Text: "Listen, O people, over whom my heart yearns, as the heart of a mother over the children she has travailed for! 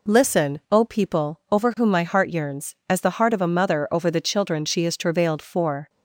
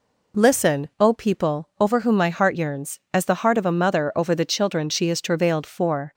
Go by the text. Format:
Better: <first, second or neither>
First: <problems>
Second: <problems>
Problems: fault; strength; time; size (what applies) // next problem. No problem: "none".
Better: neither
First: none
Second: none